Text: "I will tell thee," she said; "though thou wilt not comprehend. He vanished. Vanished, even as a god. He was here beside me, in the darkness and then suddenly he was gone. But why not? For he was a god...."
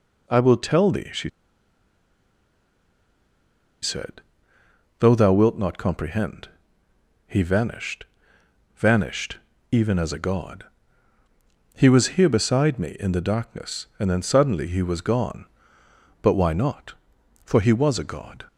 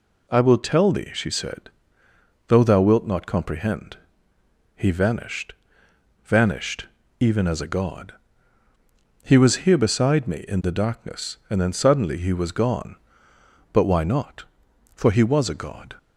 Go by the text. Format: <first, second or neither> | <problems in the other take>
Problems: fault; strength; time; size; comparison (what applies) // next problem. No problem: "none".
second | pauses between "she" and "said"; strong; at 1.2 s; 2.5 s long